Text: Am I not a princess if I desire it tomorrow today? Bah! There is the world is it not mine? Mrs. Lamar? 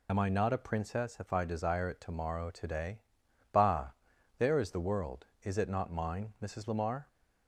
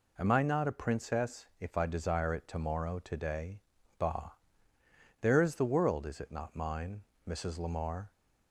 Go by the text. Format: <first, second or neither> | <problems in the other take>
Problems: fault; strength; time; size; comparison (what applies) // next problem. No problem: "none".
second | loses the start of "Am"; at 0.0 s; 35 ms